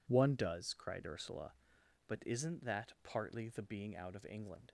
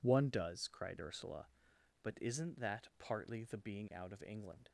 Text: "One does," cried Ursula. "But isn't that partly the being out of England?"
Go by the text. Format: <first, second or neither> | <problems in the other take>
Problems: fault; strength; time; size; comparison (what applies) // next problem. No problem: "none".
neither | none